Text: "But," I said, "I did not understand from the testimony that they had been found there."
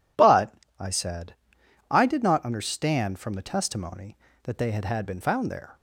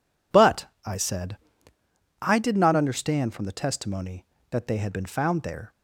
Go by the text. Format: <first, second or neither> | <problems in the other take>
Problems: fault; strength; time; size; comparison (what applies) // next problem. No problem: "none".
second | says "had" twice; at 4.8 s